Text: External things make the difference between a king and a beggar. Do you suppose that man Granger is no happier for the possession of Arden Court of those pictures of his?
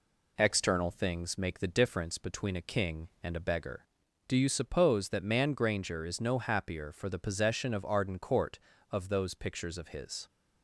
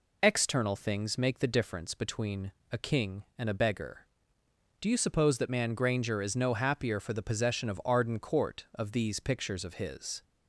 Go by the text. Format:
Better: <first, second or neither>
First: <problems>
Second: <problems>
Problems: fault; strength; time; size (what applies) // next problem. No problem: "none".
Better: first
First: none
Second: pauses between "between" and "a"; slight; at 2.5 s; 0.20 s long // says "these" for "those"; at 8.9 s